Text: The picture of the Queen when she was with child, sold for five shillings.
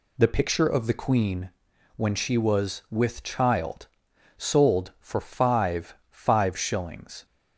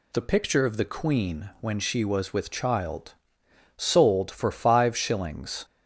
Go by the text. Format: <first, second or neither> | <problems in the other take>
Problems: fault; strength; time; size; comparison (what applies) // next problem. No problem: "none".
second | pauses between "Queen" and "when"; noticeable; at 1.4 s; 0.48 s long // says "five" twice; at 6.1 s